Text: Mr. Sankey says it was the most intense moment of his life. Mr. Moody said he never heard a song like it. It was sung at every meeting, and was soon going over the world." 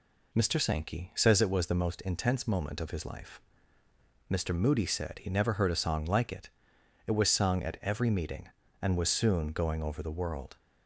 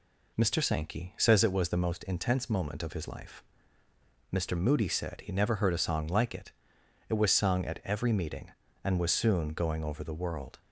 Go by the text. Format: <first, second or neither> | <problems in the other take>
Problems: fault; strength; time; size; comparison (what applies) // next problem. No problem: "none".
neither | none